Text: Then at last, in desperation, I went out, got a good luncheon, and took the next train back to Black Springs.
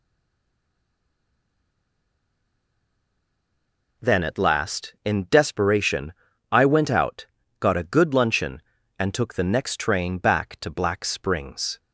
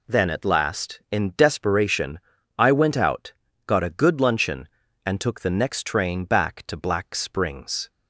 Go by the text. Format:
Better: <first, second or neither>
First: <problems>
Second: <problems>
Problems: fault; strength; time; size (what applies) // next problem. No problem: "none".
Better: second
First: stays silent before the first word; strong; until 3.9 s; 3.9 s long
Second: none